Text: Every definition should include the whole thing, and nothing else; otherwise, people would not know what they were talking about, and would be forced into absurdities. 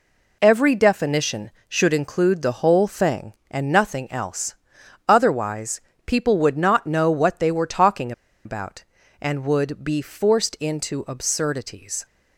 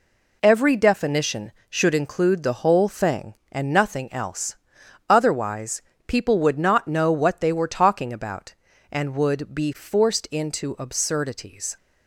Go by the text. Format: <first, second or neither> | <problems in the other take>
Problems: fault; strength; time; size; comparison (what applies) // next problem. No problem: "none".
second | pauses between "talking" and "about"; slight; at 8.1 s; 0.32 s long